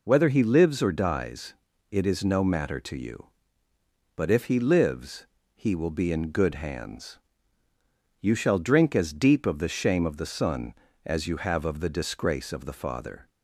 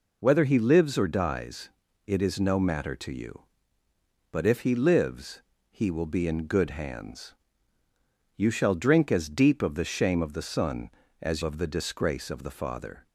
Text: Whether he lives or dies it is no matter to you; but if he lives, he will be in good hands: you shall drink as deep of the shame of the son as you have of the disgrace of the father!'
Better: first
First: pauses between "dies" and "it"; slight; at 1.5 s; 0.36 s long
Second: pauses between "dies" and "it"; slight; at 1.6 s; 0.36 s long // skips "you have"; at 11.4 s

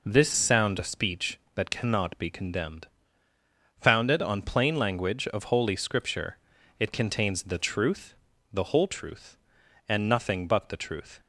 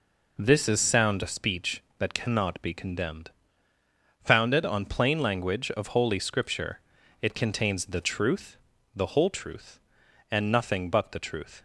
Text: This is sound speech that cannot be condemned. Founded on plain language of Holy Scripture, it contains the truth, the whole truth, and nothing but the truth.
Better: second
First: skips "is"; at 0.3 s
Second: none

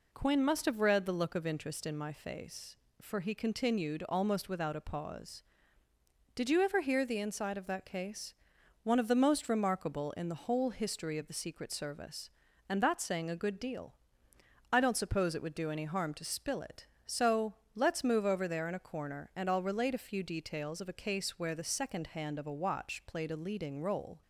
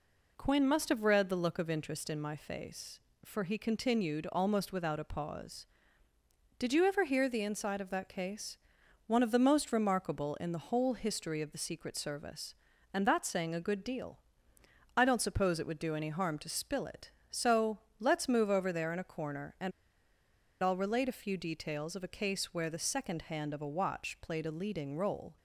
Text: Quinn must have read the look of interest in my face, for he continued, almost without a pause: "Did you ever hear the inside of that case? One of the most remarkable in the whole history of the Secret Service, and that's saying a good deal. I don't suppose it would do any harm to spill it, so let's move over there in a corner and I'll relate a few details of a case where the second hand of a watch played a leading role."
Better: first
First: pauses between "so" and "let's"; slight; at 17.5 s; 0.20 s long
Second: pauses between "so" and "let's"; slight; at 17.7 s; 0.20 s long // pauses between "and" and "I'll"; noticeable; at 19.7 s; 0.91 s long

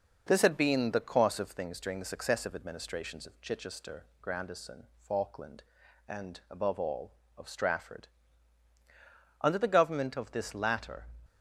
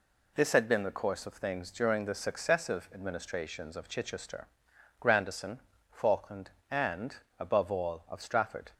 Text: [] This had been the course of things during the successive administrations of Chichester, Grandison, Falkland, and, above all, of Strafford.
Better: second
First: goes on to say "Under the government of this latter"; strong; from 9.3 s on; 1.6 s long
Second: none

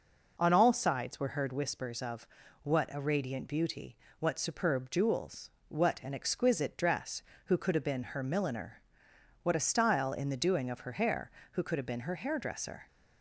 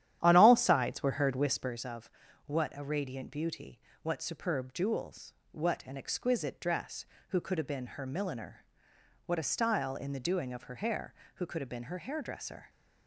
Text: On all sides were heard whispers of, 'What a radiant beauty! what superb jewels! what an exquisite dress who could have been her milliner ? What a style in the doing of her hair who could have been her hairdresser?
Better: first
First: none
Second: starts louder than the rest; strong; until 1.9 s; 11 dB

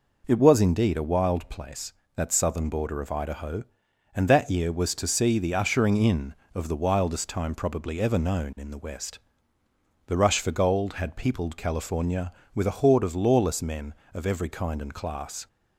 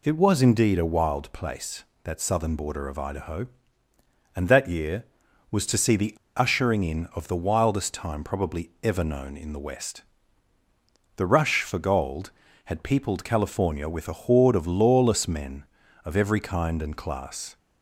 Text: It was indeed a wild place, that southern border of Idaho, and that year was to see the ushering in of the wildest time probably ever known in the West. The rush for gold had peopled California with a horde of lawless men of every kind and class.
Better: first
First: none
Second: pauses between "the" and "ushering"; slight; at 6.1 s; 0.22 s long

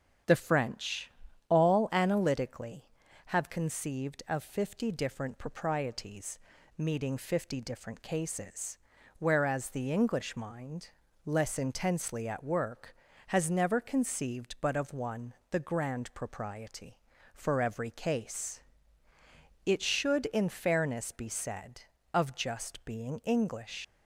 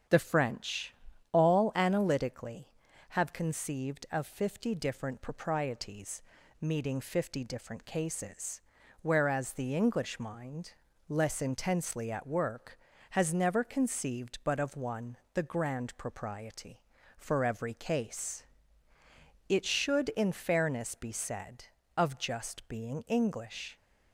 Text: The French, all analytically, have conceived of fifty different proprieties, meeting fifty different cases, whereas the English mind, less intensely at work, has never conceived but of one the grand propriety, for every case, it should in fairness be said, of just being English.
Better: second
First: starts louder than the rest; strong; until 1.6 s; 8 dB // pauses between "one" and "the"; slight; at 15.3 s; 0.18 s long // leaves "English" unfinished; at 23.8 s; 75 ms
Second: starts louder than the rest; strong; until 1.4 s; 8 dB // pauses between "one" and "the"; slight; at 15.1 s; 0.18 s long

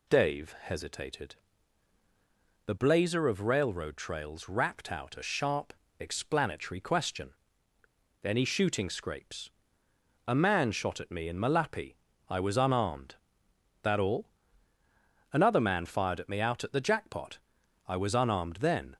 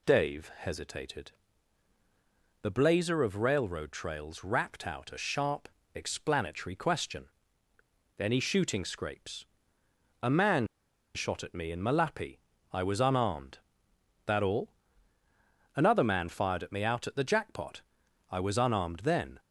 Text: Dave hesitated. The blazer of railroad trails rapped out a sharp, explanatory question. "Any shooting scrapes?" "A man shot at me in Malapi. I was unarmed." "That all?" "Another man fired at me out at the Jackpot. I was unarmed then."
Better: first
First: none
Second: pauses between "man" and "shot"; noticeable; at 10.6 s; 0.48 s long

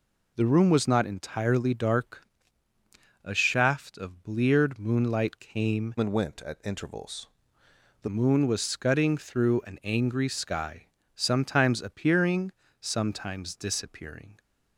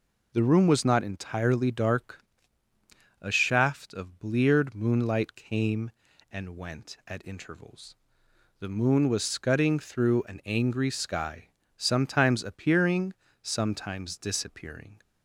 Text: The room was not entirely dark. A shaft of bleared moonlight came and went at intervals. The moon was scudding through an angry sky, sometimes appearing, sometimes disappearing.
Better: second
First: changes voice from "and" to "The"; from 5.9 to 8.0 s; 2.1 s long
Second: none

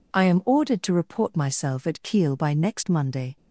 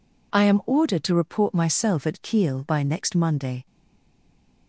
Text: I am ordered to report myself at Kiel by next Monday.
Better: first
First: none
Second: stays silent after the last word; from 3.6 s on; 1.0 s long

